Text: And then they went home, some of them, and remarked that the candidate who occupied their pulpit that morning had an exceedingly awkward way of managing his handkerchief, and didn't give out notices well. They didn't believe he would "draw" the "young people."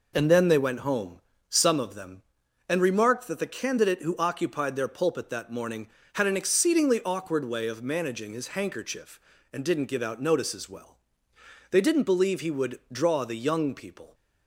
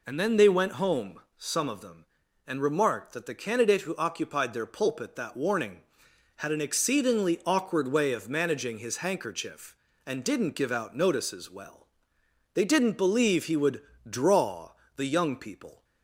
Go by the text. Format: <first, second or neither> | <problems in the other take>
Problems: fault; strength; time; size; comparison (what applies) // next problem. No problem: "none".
first | says "warning" for "morning"; at 5.3 s // pauses between "would" and "draw"; slight; at 13.8 s; 0.28 s long // pauses between "draw" and "the"; slight; at 14.7 s; 0.24 s long